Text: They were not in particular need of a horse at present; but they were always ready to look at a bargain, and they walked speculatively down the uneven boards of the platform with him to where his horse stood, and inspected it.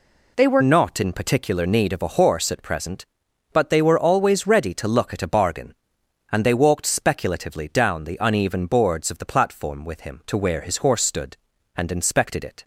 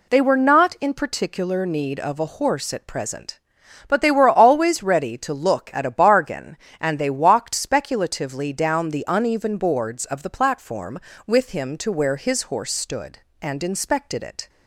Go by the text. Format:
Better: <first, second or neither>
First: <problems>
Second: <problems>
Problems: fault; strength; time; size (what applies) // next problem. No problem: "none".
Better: second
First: changes voice at "not"; from 0.6 s on; 12.0 s long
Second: none